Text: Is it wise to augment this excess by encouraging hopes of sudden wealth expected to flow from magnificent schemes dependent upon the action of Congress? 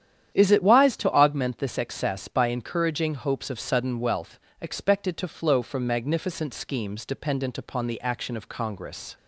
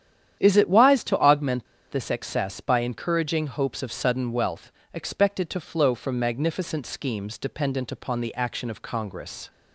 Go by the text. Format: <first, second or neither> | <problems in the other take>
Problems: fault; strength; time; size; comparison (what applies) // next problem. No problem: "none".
first | starts louder than the rest; strong; until 1.4 s; 10 dB; strong in the first // pauses between "augment" and "this"; slight; at 1.6 s; 0.26 s long // pauses between "wealth" and "expected"; slight; at 4.7 s; 0.22 s long; slight in the first